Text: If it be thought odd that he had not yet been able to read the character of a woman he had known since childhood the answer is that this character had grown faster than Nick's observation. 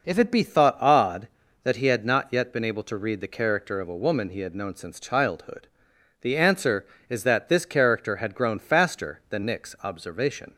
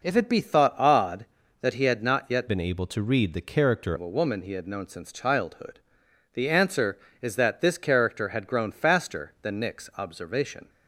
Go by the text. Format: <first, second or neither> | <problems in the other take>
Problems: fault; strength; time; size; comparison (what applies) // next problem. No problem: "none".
first | changes voice from "been" to "character"; from 2.4 to 3.9 s; 1.5 s long // pauses between "childhood" and "the"; noticeable; at 5.7 s; 0.54 s long; noticeable in the first